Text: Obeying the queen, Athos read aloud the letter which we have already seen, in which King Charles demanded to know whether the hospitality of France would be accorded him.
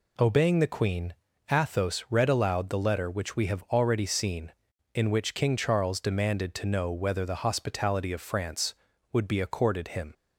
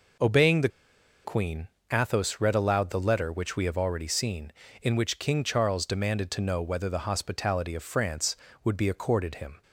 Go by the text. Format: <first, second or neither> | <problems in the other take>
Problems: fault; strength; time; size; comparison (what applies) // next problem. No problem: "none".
first | pauses between "the" and "queen"; noticeable; at 0.6 s; 0.55 s long